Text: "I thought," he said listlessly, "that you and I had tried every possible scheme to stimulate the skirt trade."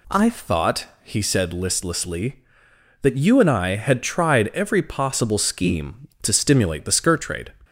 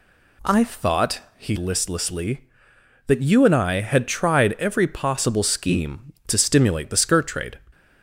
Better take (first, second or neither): first